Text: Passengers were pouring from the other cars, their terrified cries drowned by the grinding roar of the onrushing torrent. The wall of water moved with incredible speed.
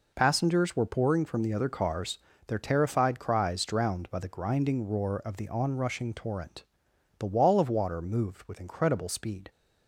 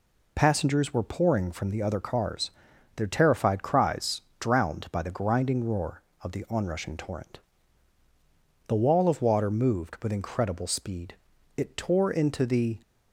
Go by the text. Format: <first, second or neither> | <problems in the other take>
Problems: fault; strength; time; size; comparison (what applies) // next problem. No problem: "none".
first | pauses between "cries" and "drowned"; slight; at 4.2 s; 0.18 s long // goes on to say "It tore into the"; noticeable; from 11.5 s on; 1.2 s long